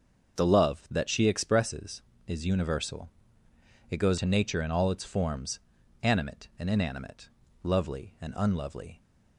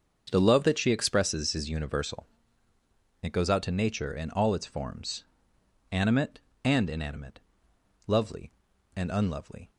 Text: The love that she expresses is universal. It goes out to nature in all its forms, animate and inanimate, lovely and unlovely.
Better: second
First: starts louder than the rest; until 1.4 s; 6.5 dB // skips "out"; at 4.1 s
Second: starts louder than the rest; until 1.3 s; 6.5 dB

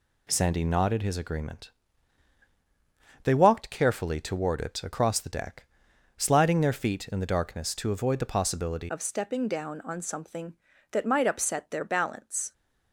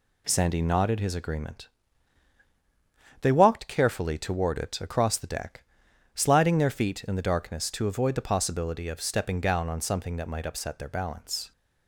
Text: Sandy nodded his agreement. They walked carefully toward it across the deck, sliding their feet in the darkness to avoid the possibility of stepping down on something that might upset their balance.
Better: second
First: changes voice at "of"; from 8.8 s on; 3.7 s long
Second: none

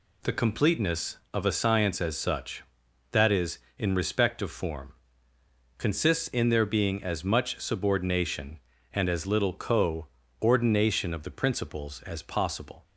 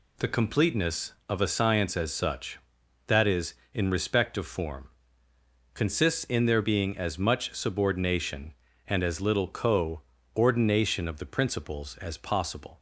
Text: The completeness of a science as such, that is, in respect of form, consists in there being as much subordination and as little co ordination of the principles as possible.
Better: neither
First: pauses between "co" and "ordination"; slight; at 10.0 s; 0.34 s long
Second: pauses between "co" and "ordination"; slight; at 10.0 s; 0.34 s long

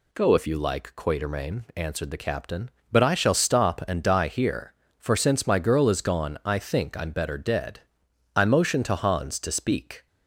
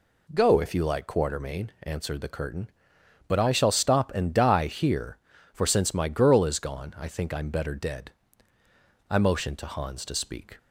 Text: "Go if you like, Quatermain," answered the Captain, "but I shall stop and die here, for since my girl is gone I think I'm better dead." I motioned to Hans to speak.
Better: first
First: none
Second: says "Curtain" for "Captain"; at 2.2 s

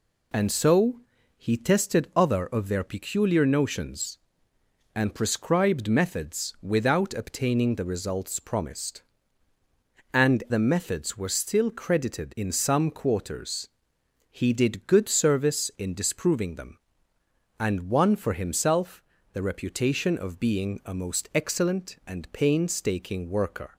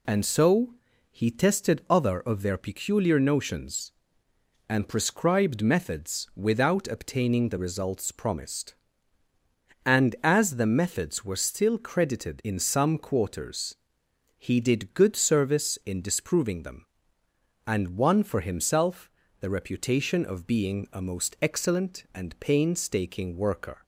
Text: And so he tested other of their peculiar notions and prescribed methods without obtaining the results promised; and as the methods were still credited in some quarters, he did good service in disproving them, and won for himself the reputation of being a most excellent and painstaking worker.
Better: second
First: pauses between "so" and "he"; at 0.9 s; 0.40 s long // skips "as"; at 10.4 s // pauses between "himself" and "the"; slight; at 19.0 s; 0.30 s long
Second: pauses between "so" and "he"; at 0.7 s; 0.40 s long // pauses between "himself" and "the"; slight; at 19.0 s; 0.30 s long

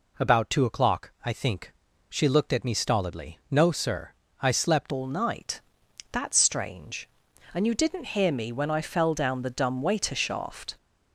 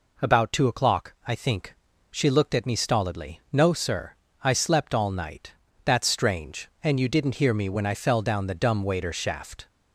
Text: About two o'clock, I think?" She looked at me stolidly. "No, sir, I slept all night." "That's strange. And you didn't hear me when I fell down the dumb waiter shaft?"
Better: second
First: changes voice at "all"; from 4.9 s on; 5.8 s long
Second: none

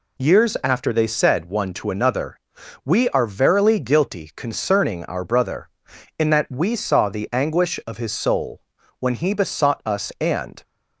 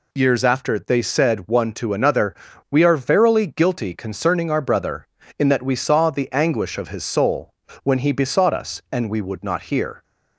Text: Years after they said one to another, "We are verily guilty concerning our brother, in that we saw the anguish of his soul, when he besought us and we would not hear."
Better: second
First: stops before "we would not hear"; at 10.6 s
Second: none

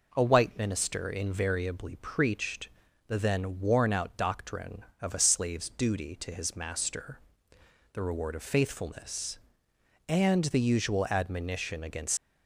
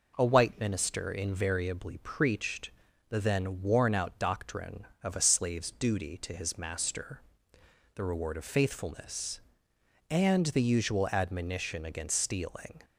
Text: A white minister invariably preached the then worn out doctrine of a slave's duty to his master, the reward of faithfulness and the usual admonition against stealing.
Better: second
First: pauses between "preached" and "the"; at 2.6 s; 0.38 s long // stops before "stealing"; at 12.1 s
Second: pauses between "preached" and "the"; at 2.7 s; 0.38 s long

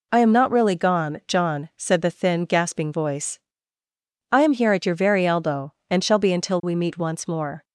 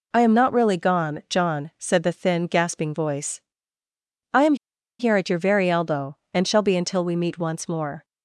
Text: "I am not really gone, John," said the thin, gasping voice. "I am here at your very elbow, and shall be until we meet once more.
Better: first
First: none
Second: pauses between "am" and "here"; at 4.5 s; 0.44 s long

